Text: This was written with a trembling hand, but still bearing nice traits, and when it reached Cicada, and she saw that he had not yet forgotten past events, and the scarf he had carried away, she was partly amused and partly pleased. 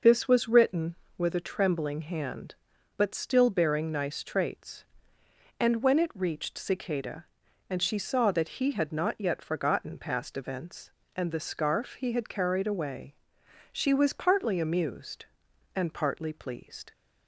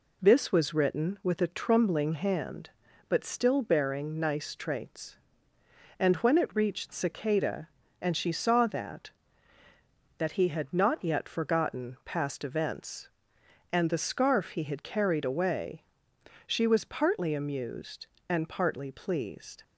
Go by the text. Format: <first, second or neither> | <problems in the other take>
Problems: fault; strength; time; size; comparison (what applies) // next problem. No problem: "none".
first | says "that" twice; at 10.1 s